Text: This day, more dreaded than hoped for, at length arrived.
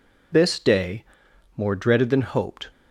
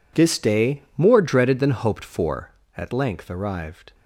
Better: second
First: stops before "for at length arrived"; at 2.7 s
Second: none

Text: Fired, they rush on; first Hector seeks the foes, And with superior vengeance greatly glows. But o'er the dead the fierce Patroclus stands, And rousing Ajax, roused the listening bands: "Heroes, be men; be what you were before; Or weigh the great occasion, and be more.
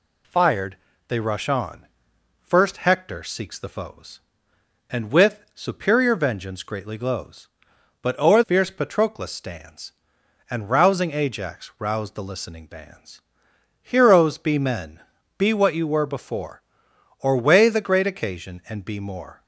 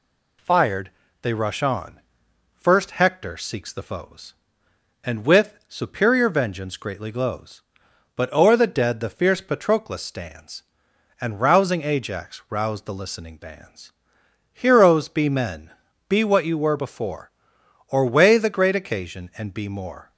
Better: second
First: skips "the dead the"; at 8.4 s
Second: none

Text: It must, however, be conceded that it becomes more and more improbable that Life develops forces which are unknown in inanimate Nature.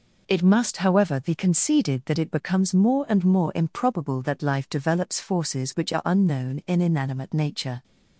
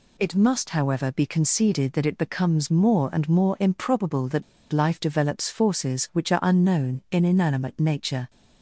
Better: first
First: none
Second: pauses between "that" and "Life"; slight; at 4.4 s; 0.28 s long

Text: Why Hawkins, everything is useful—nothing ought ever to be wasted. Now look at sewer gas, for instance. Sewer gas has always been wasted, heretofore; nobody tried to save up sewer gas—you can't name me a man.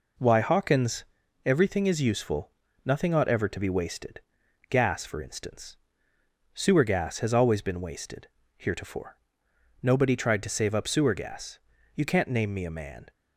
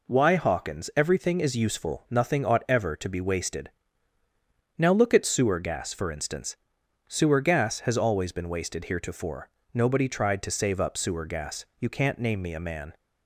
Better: second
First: skips "Now look at sewer"; at 4.4 s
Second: none

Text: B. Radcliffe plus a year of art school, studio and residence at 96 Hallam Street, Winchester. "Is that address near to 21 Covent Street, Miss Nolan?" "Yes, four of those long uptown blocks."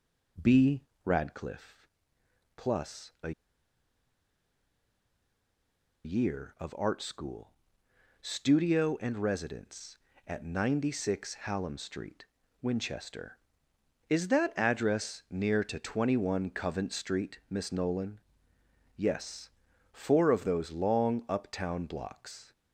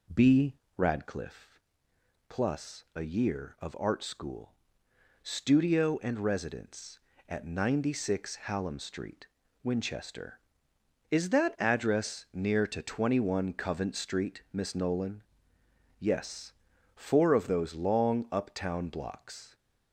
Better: second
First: pauses between "Radcliffe" and "plus"; noticeable; at 1.8 s; 0.68 s long // pauses between "a" and "year"; strong; at 3.3 s; 2.7 s long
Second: pauses between "Radcliffe" and "plus"; noticeable; at 1.6 s; 0.68 s long

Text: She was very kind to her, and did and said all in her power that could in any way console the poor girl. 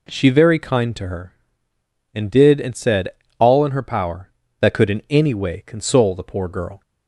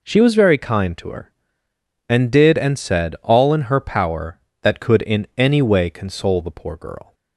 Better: second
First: skips "was"; at 0.2 s // pauses between "said" and "all"; slight; at 3.0 s; 0.30 s long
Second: none

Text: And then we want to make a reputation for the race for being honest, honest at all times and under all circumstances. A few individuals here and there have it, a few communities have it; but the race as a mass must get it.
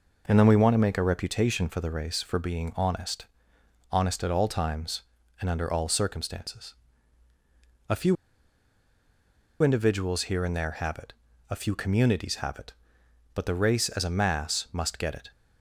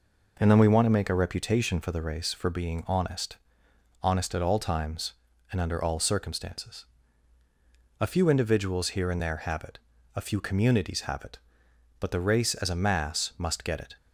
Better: second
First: pauses between "few" and "individuals"; strong; at 8.1 s; 1.4 s long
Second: none

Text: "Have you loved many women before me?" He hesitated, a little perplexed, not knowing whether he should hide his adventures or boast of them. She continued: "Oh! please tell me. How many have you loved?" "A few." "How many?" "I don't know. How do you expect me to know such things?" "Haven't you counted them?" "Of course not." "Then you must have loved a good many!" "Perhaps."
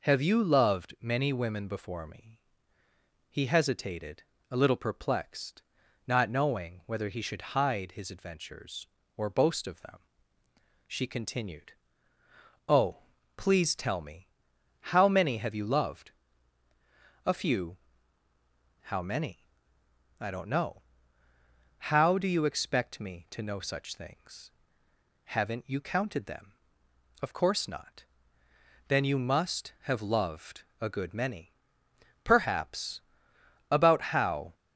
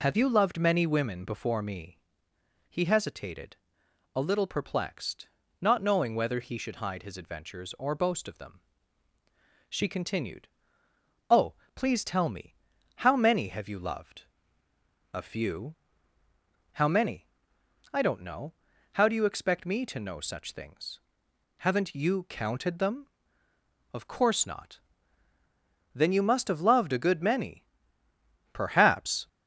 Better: second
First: pauses between "loved" and "a"; slight; at 30.6 s; 0.18 s long // goes on to say "About how"; noticeable; from 33.6 s on; 0.84 s long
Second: none

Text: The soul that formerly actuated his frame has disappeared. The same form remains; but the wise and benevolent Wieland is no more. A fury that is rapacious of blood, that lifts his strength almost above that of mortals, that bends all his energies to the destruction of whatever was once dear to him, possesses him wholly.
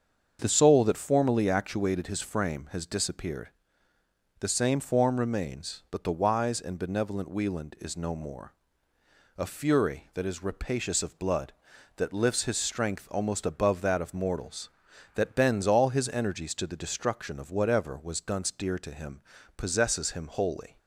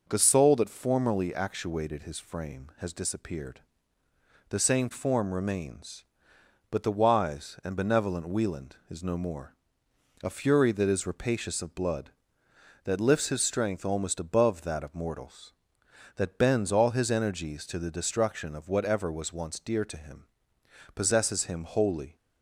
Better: second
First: starts louder than the rest; until 1.4 s; 7 dB // says "dunce" for "once"; at 18.1 s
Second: none

